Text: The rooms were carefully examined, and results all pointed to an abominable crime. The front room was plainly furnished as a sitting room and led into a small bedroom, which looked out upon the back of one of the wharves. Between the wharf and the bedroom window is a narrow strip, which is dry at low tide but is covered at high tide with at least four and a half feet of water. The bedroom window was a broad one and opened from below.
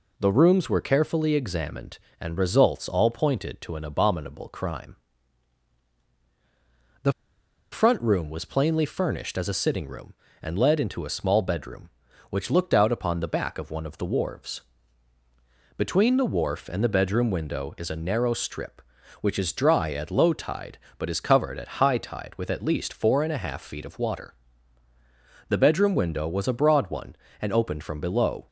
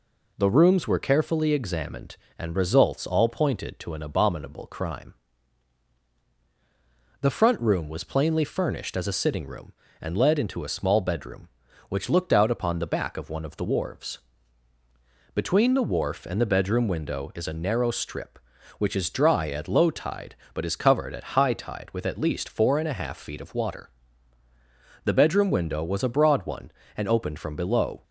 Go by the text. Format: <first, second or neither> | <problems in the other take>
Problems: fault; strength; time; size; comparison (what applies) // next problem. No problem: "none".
second | pauses between "The" and "front"; noticeable; at 7.1 s; 0.60 s long